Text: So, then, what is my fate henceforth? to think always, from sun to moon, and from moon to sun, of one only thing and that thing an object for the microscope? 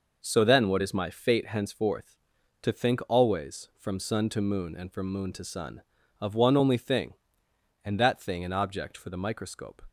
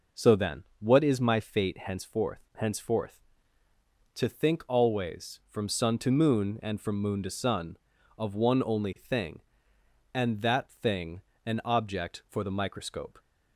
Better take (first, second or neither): first